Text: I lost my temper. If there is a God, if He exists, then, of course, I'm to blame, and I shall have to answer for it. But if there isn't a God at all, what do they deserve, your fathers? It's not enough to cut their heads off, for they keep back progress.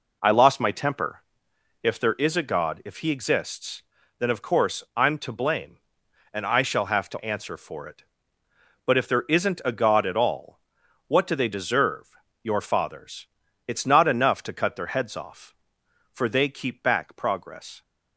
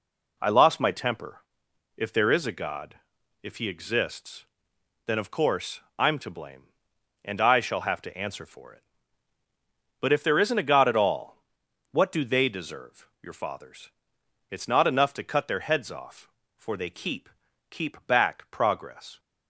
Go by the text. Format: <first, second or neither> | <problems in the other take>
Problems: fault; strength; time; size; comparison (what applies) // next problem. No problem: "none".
first | says "keep" twice; at 17.7 s